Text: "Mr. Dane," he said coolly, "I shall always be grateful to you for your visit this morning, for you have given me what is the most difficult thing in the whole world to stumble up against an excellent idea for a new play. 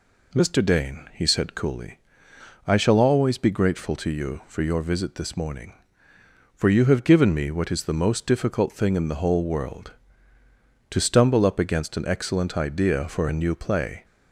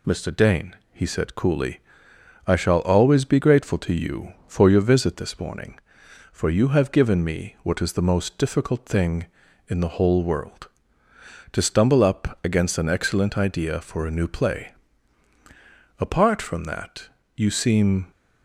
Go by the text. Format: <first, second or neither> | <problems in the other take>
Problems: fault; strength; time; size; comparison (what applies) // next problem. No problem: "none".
first | goes on to say "Apart from that you seem"; strong; from 15.9 s on; 2.1 s long